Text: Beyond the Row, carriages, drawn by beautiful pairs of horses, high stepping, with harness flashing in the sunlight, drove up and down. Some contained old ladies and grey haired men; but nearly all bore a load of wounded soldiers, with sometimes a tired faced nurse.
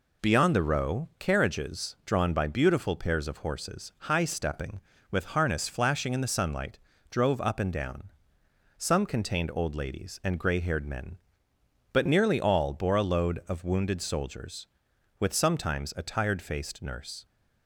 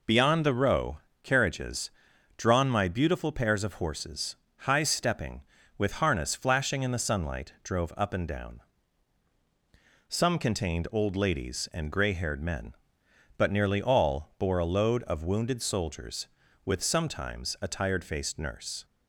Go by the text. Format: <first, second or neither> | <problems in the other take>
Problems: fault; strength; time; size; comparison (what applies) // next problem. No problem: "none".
first | says "my" for "by"; at 2.6 s